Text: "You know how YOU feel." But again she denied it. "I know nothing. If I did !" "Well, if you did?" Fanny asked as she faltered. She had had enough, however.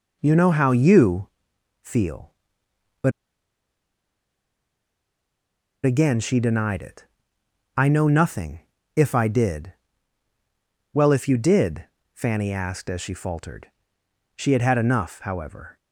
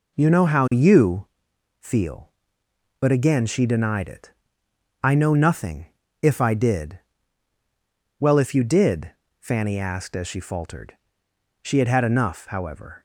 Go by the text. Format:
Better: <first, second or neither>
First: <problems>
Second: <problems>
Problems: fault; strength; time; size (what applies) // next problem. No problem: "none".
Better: second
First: pauses between "YOU" and "feel"; noticeable; at 1.2 s; 0.52 s long // pauses between "But" and "again"; strong; at 3.1 s; 2.7 s long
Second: pauses between "YOU" and "feel"; noticeable; at 1.2 s; 0.52 s long